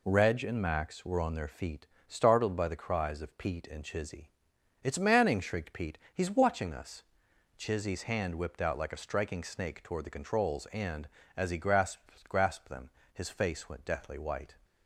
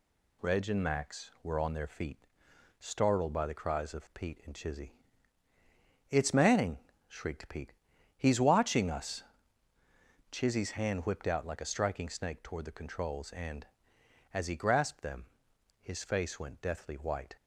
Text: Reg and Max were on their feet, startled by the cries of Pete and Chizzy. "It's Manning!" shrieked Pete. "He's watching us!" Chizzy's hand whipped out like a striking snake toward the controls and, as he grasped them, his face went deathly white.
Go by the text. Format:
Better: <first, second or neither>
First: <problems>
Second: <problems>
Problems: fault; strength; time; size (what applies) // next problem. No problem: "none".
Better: second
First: says "grasped" twice; at 12.2 s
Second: none